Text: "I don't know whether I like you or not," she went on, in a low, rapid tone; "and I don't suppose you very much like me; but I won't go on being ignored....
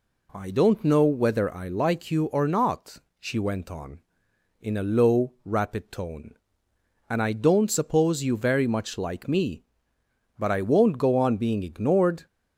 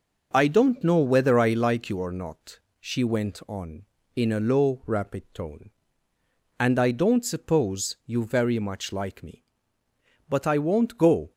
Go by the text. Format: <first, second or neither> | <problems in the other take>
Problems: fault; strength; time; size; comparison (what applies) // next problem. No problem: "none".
first | stops before "on being ignored"; at 11.3 s